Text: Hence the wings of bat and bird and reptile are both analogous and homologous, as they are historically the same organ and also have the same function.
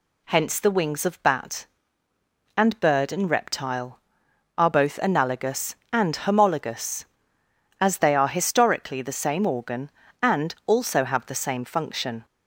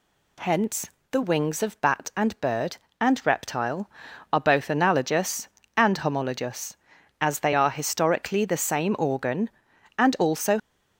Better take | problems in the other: first | pauses between "Hence" and "the"; slight; at 0.8 s; 0.22 s long // stops before "have the same function"; at 10.5 s

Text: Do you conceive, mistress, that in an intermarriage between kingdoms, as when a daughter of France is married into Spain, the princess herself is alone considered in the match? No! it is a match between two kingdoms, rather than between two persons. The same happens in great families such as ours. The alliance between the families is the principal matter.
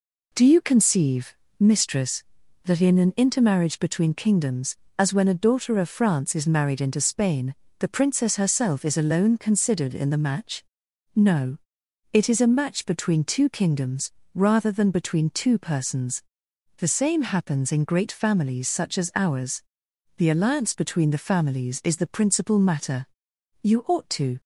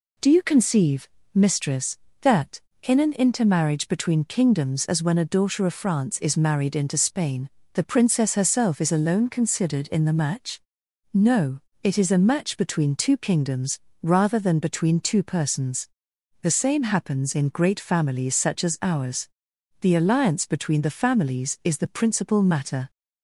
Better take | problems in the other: second | goes on to say "You ought to"; noticeable; from 23.6 s on; 0.78 s long

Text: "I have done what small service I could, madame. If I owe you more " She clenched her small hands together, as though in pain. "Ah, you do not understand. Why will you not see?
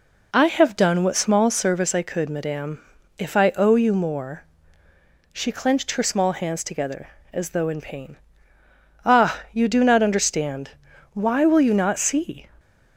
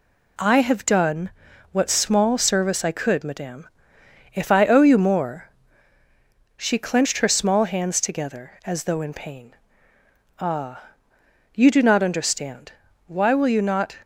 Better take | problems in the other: first | pauses between "done" and "what"; at 1.3 s; 0.42 s long // stops before "see"; at 14.0 s

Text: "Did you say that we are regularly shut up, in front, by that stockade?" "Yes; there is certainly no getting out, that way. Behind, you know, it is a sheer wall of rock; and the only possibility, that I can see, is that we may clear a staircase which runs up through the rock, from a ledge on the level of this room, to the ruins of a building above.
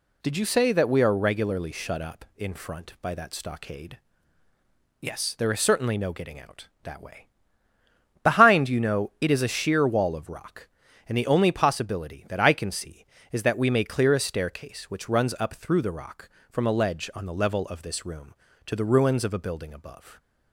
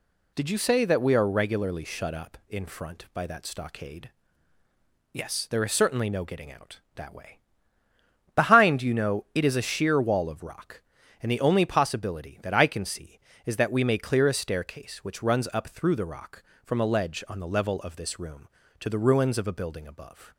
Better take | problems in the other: neither | none

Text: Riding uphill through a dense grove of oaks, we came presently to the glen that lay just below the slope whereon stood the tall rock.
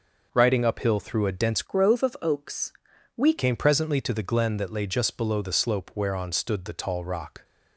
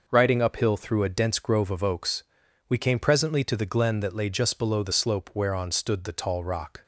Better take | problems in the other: second | changes voice from "grove" to "we"; from 1.6 to 3.3 s; 1.7 s long

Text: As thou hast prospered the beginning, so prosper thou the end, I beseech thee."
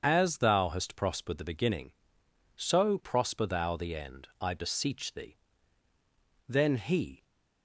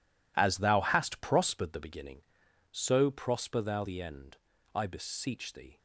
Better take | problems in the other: second | starts louder than the rest; strong; until 1.0 s; 7 dB // goes on to say "Then he"; noticeable; from 6.4 s on; 0.76 s long

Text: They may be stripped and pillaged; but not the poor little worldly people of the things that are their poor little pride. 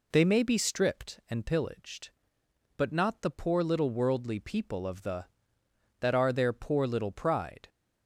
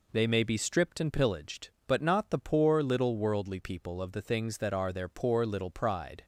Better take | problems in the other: second | skips "things"; at 5.6 s

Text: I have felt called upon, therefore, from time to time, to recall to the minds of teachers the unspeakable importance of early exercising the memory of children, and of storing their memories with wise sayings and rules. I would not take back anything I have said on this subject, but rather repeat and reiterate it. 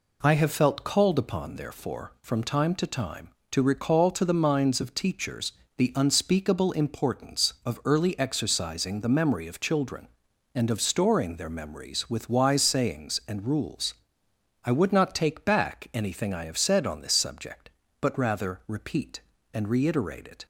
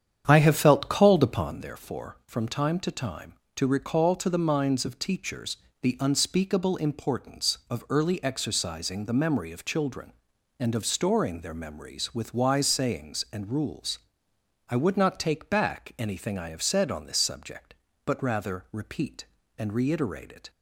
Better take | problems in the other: first | starts louder than the rest; strong; until 1.7 s; 8.5 dB // pauses between "teachers" and "the"; slight; at 5.5 s; 0.26 s long; slight in the first

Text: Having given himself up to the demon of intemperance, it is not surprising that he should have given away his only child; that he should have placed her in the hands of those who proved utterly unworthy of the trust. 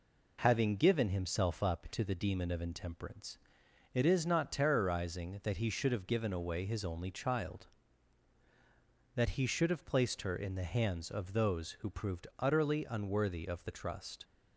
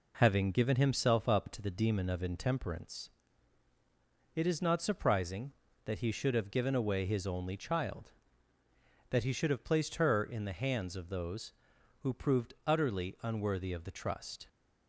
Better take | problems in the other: second | says "terrorizing" for "surprising"; at 4.5 s

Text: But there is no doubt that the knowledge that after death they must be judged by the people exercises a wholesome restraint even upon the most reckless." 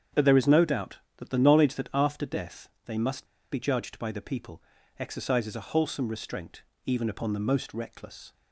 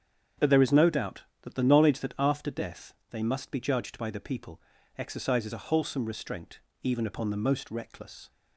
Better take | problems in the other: second | starts louder than the rest; strong; until 1.3 s; 8 dB; strong in the second // pauses between "death" and "they"; slight; at 2.6 s; 0.16 s long; slight in the second // pauses between "must" and "be"; slight; at 3.2 s; 0.26 s long // pauses between "people" and "exercises"; at 4.6 s; 0.38 s long; also in the second // pauses between "restraint" and "even"; slight; at 6.6 s; 0.22 s long; slight in the second

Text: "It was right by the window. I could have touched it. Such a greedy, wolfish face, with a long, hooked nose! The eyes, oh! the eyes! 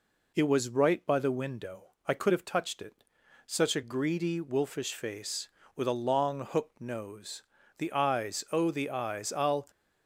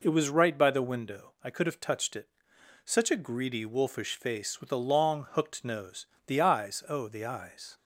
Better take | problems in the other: second | goes on to say "I'll"; slight; from 9.3 s on; 0.34 s long

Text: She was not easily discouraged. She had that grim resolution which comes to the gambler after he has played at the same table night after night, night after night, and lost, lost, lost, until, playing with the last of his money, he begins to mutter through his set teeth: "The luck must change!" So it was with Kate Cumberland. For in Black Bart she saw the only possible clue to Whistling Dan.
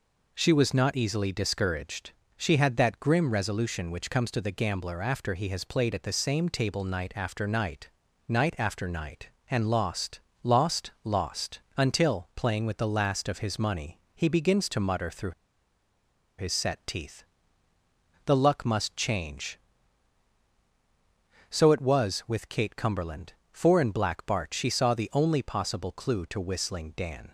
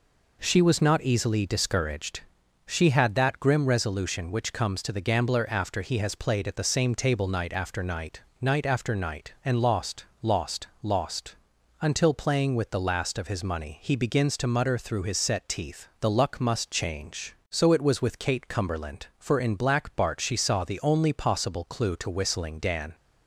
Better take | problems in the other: second | pauses between "through" and "his"; at 15.3 s; 1.0 s long

